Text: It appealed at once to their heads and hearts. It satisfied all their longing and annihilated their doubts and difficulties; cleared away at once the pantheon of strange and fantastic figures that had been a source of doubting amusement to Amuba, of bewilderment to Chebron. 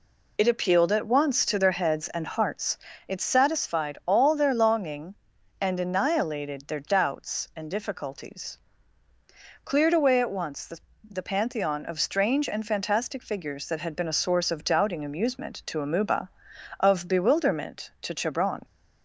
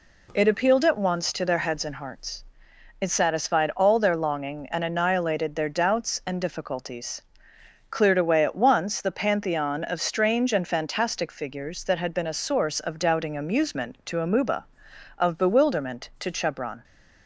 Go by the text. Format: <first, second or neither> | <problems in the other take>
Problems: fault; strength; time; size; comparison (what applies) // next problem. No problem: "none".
second | says "the" twice; at 11.0 s